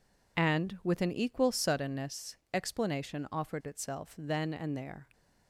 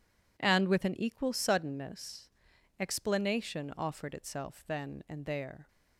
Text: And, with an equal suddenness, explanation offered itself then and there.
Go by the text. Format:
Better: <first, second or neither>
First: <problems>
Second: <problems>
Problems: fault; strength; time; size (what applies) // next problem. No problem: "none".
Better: neither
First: none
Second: none